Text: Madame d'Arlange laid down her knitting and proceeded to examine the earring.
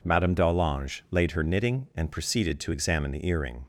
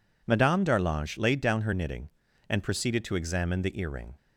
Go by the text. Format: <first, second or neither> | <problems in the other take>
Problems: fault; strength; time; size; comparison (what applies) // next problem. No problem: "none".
second | skips "down"; at 1.2 s